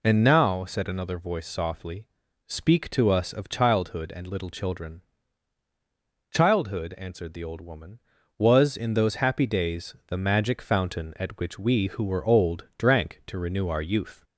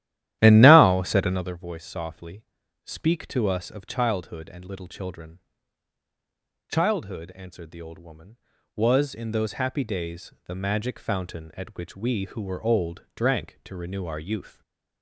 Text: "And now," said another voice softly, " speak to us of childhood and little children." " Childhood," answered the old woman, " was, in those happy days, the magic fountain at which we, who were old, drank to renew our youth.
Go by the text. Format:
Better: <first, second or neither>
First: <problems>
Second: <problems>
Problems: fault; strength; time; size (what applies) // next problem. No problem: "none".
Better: first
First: none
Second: starts louder than the rest; strong; until 1.6 s; 13.5 dB // stays silent after the last word; slight; from 14.4 s on; 0.6 s long